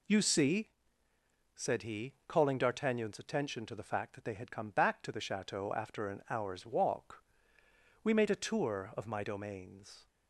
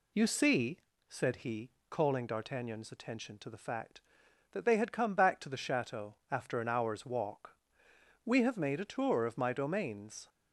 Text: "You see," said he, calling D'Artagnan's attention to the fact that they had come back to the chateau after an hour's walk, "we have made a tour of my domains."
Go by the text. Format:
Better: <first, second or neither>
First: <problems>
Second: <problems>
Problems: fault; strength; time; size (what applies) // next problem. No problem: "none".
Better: second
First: skips "have"; at 8.1 s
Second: none